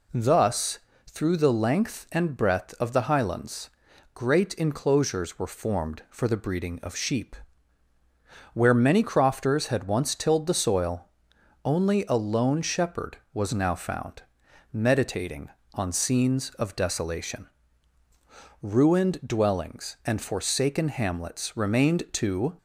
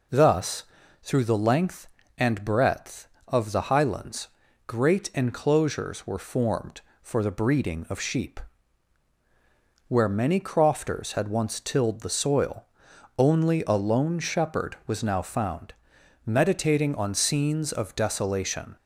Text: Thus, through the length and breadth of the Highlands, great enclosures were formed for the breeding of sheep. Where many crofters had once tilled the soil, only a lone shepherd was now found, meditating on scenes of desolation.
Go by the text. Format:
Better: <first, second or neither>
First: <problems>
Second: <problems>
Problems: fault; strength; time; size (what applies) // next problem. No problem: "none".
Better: second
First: goes on to say "Ruined dwellings and forsaken hamlets remained to"; strong; from 18.6 s on; 3.9 s long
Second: none